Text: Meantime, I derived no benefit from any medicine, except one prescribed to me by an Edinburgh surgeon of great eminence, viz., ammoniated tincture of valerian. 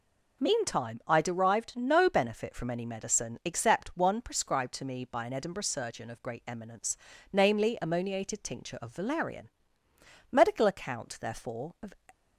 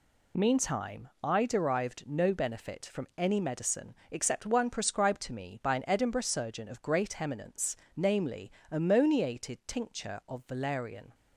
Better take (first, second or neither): second